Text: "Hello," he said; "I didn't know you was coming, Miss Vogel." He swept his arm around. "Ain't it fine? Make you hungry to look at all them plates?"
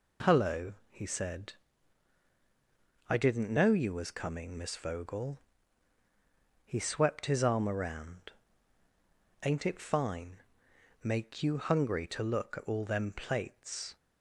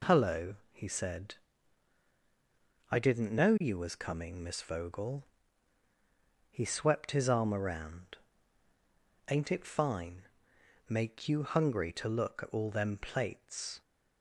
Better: neither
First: none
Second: none

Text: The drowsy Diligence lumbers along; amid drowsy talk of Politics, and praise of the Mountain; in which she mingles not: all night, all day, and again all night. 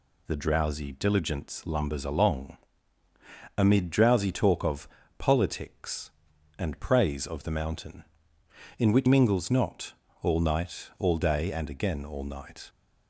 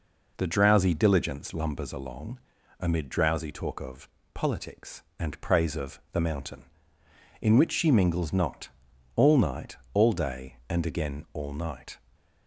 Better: second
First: pauses between "of" and "Politics"; slight; at 4.8 s; 0.30 s long // skips "she"; at 9.0 s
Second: pauses between "of" and "Politics"; slight; at 4.0 s; 0.26 s long

